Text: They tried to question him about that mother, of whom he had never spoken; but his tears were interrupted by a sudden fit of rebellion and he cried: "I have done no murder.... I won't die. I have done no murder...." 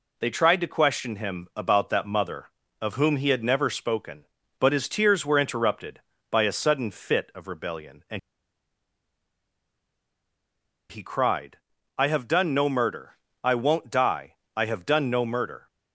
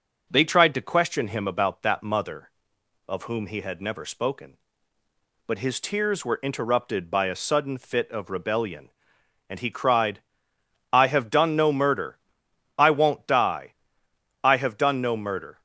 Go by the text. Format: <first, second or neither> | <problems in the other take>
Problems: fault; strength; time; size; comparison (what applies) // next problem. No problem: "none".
second | pauses between "and" and "he"; strong; at 8.1 s; 2.7 s long